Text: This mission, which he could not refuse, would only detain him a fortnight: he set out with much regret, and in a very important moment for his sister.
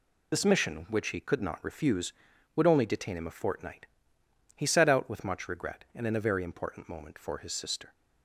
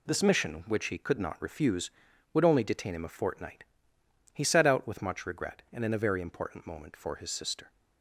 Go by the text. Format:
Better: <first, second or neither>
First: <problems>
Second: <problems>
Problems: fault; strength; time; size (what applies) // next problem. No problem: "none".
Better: second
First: loses the start of "This"; at 0.3 s; 35 ms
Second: none